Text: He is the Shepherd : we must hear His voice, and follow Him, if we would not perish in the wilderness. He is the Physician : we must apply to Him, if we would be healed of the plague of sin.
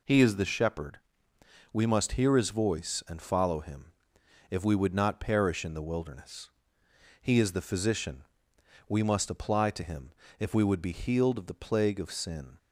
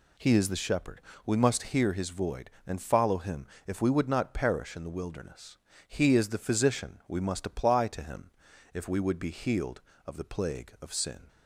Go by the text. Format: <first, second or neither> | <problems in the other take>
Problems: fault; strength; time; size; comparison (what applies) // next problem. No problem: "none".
first | says "void" for "voice"; at 2.0 s